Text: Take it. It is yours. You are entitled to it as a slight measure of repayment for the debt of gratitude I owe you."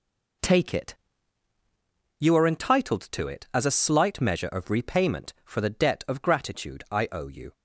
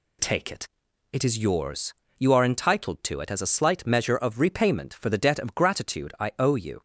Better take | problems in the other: second | skips "It is yours"; at 1.5 s

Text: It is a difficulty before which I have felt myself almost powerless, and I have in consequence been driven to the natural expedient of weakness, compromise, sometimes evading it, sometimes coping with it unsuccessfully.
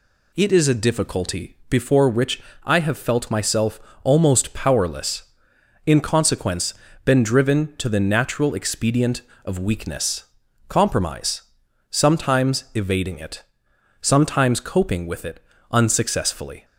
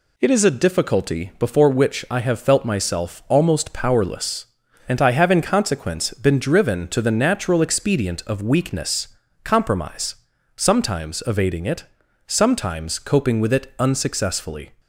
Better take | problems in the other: second | pauses between "which" and "I"; slight; at 2.4 s; 0.22 s long // pauses between "myself" and "almost"; slight; at 3.7 s; 0.24 s long // skips "and I have"; at 5.5 s // pauses between "consequence" and "been"; slight; at 6.7 s; 0.32 s long // pauses between "it" and "unsuccessfully"; slight; at 15.3 s; 0.32 s long

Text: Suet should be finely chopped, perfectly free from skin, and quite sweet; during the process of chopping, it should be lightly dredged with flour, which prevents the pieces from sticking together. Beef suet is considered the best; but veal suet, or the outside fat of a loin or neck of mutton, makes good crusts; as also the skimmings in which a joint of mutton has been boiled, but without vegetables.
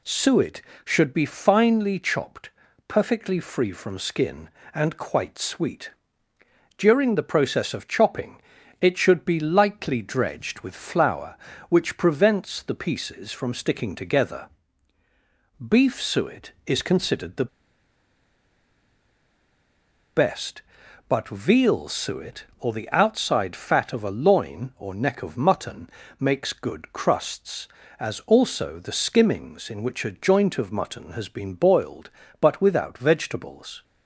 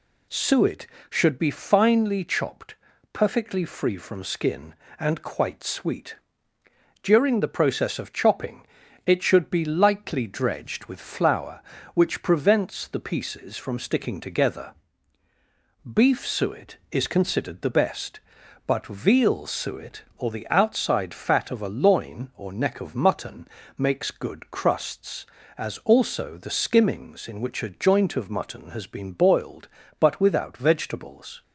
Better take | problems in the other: second | pauses between "the" and "best"; strong; at 17.4 s; 2.6 s long

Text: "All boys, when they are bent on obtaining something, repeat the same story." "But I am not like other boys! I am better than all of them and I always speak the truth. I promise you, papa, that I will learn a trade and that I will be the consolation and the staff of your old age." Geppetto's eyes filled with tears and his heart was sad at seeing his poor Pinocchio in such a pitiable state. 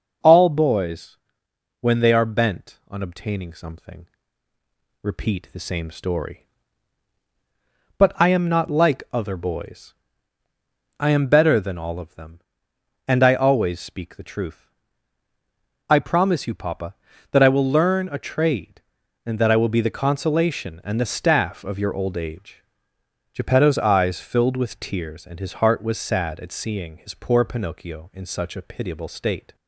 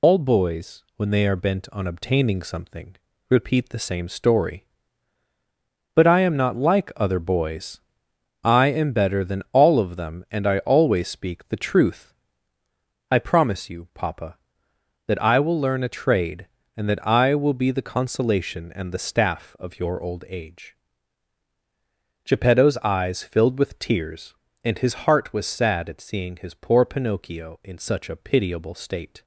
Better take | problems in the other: first | loses the start of "All"; at 0.0 s; 100 ms

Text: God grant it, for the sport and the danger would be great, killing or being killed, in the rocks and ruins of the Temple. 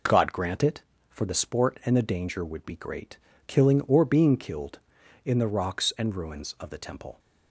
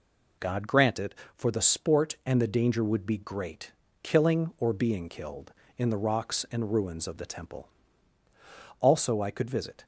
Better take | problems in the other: first | goes on to say "Also I could visit"; noticeable; from 8.8 s on; 1.0 s long

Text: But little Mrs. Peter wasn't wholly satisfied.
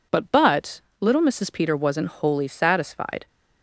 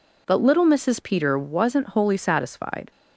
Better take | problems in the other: second | says "But" twice; at 0.3 s

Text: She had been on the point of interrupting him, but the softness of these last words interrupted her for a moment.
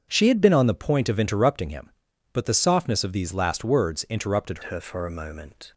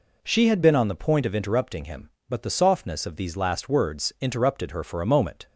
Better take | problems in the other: second | starts louder than the rest; strong; until 1.1 s; 7.5 dB // changes voice at "her"; from 4.6 s on; 1.1 s long

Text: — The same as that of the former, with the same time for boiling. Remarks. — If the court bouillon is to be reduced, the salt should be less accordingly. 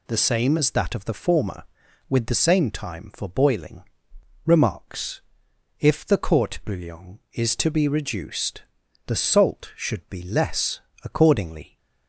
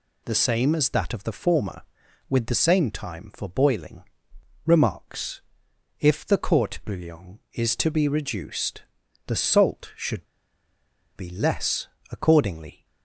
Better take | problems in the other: first | pauses between "should" and "be"; noticeable; at 10.2 s; 0.90 s long // pauses between "less" and "accordingly"; slight; at 11.8 s; 0.24 s long; slight in the first

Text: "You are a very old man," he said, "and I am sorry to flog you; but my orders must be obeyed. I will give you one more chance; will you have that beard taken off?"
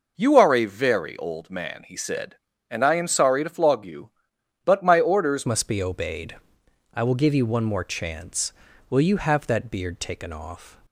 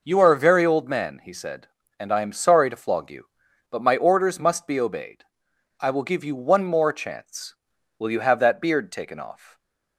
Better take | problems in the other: second | changes voice at "must"; from 5.4 s on; 5.3 s long

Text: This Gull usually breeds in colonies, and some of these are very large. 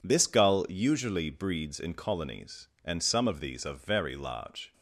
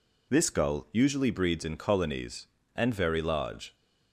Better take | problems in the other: first | skips "some of these are"; at 2.9 s

